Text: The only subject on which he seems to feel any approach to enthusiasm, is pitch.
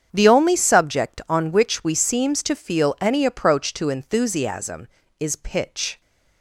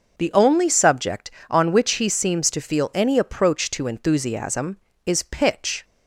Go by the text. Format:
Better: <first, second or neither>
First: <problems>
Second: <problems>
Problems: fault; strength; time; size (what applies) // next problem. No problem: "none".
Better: second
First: starts louder than the rest; strong; until 1.1 s; 7.5 dB // says "we" for "he"; at 1.8 s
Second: starts louder than the rest; noticeable; until 1.1 s; 6 dB